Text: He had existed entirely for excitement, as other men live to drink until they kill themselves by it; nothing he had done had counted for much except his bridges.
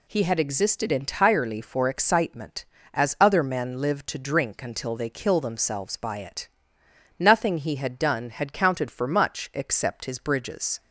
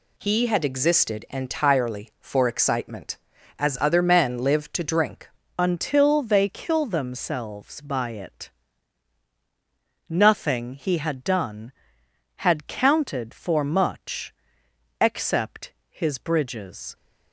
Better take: first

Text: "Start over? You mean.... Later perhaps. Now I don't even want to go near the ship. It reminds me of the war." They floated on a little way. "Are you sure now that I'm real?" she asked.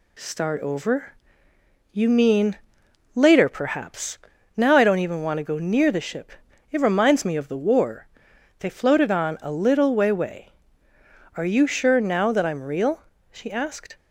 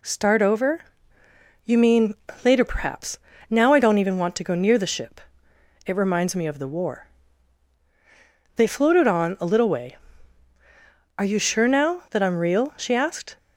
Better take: second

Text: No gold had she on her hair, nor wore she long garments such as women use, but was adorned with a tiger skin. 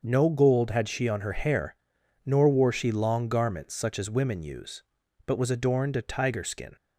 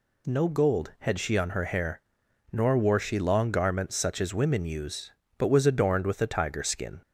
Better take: second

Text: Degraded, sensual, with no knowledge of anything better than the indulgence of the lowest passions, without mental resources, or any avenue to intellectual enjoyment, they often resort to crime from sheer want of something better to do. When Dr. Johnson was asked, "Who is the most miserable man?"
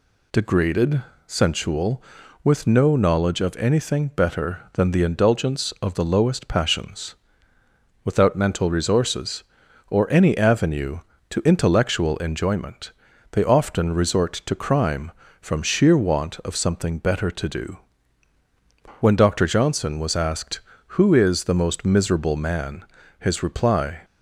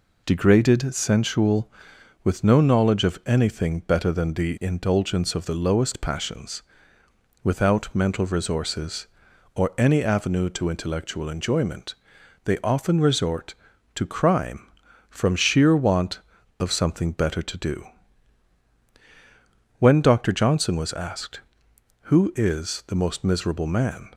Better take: second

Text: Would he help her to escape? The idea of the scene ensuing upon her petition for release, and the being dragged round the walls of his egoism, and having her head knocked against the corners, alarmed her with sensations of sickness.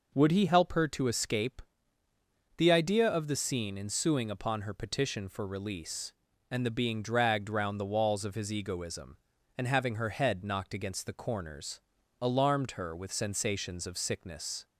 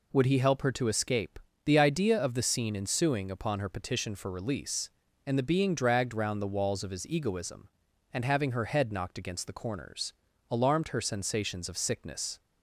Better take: first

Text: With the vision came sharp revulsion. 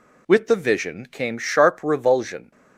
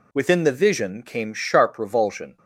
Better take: first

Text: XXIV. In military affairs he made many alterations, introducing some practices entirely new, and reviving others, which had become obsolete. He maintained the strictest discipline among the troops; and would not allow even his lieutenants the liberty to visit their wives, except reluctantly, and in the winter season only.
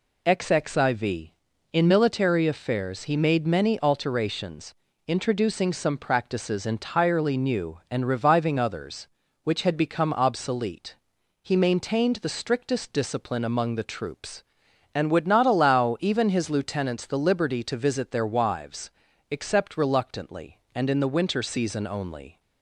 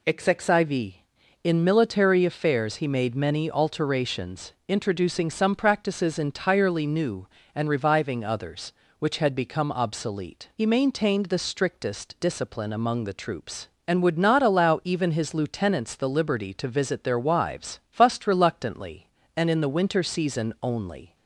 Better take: first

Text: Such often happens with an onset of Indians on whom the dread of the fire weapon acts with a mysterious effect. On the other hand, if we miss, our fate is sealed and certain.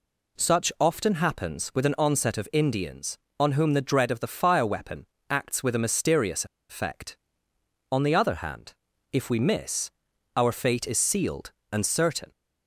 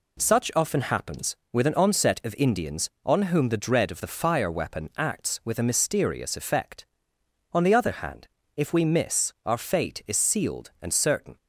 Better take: second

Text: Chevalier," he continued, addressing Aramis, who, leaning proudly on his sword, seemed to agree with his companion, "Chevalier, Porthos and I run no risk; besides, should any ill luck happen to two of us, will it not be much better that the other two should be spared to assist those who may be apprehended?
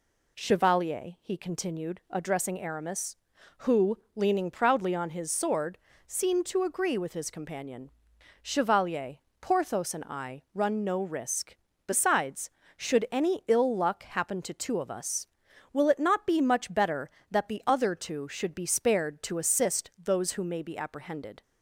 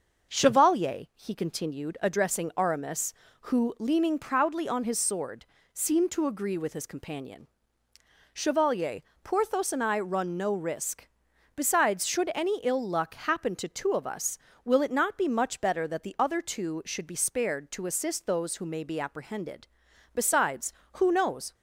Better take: first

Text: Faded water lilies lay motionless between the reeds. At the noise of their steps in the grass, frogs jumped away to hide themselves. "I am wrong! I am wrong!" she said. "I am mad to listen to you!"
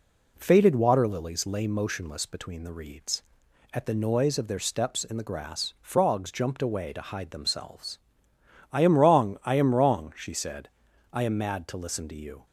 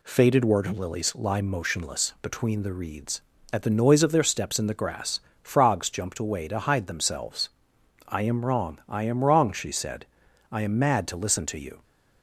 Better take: first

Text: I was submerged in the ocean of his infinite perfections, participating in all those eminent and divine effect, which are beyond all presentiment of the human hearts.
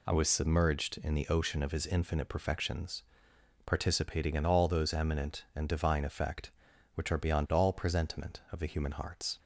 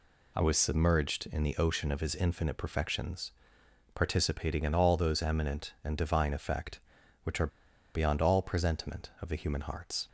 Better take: first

